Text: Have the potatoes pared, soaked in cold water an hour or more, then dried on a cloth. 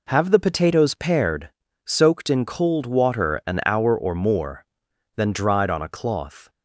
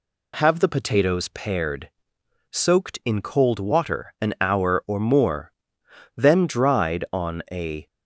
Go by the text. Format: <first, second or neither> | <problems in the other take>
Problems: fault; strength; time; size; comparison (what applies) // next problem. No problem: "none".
first | stops before "cloth"; at 7.8 s